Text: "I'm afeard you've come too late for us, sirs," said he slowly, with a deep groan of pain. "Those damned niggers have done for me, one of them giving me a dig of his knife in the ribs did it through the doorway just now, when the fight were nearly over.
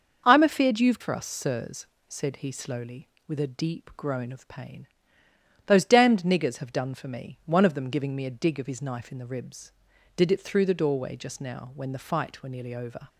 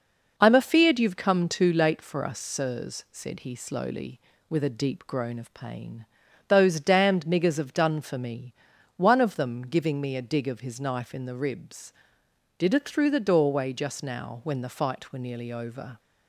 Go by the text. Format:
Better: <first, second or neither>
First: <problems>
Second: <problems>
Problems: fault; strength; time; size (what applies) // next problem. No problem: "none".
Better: second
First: starts louder than the rest; until 1.2 s; 6 dB // skips "come too late"; at 1.0 s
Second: none